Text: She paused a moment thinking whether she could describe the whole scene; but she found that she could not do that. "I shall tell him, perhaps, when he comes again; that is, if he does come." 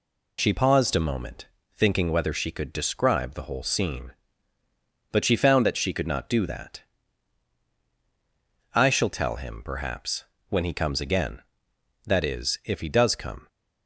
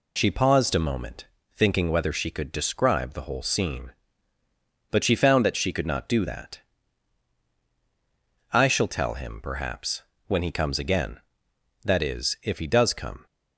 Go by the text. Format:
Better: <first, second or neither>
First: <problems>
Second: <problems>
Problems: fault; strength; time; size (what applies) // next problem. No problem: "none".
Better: neither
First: pauses between "moment" and "thinking"; slight; at 1.4 s; 0.28 s long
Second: pauses between "moment" and "thinking"; slight; at 1.2 s; 0.28 s long